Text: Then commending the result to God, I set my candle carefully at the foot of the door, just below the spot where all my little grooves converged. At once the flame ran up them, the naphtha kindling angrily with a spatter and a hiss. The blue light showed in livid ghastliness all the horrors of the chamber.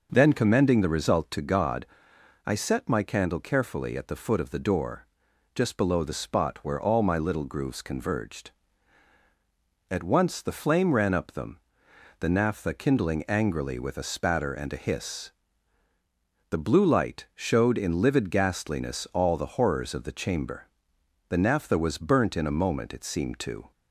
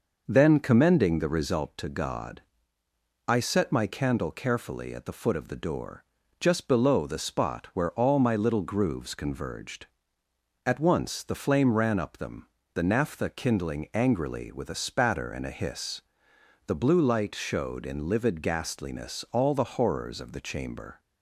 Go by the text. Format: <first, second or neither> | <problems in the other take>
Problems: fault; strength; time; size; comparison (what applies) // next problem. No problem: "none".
second | goes on to say "The naphtha was burnt in a moment it seemed to"; strong; from 21.2 s on; 2.4 s long